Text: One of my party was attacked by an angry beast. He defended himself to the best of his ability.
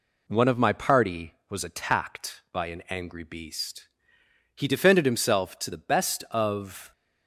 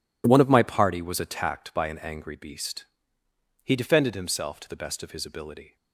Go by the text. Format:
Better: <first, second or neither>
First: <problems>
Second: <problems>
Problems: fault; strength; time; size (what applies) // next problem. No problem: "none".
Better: second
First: stops before "his ability"; at 6.9 s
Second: none